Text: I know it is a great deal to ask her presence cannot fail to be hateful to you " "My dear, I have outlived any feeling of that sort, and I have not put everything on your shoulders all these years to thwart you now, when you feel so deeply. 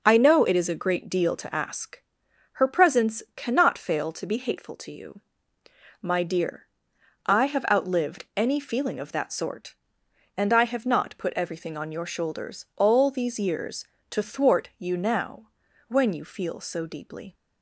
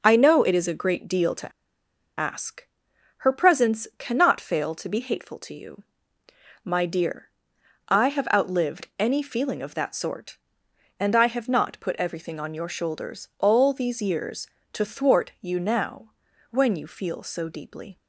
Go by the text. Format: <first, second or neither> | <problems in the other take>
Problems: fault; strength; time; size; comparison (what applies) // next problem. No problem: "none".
first | starts louder than the rest; strong; until 1.0 s; 7.5 dB; strong in the first // pauses between "to" and "ask"; noticeable; at 1.5 s; 0.68 s long // pauses between "ask" and "her"; noticeable; at 2.6 s; 0.52 s long; noticeable in the first